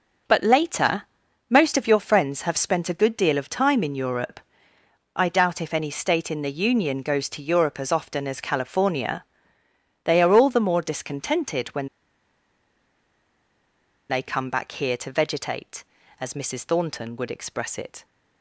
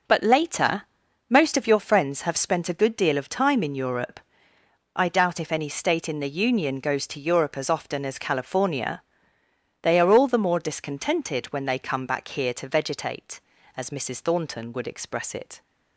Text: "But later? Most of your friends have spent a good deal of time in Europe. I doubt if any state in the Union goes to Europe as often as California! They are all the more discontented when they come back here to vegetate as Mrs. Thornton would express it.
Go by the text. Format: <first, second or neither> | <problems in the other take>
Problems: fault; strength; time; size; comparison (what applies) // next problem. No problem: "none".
second | pauses between "when" and "they"; strong; at 11.8 s; 2.2 s long